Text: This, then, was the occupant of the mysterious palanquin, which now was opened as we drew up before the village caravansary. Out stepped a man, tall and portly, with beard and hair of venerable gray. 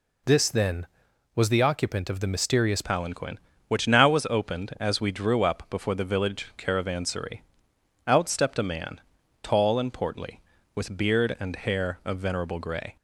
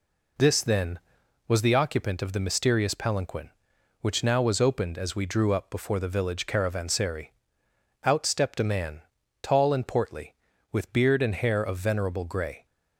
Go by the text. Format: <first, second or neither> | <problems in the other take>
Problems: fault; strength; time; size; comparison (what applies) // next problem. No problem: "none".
second | changes voice at "palanquin"; from 2.8 s on; 10.1 s long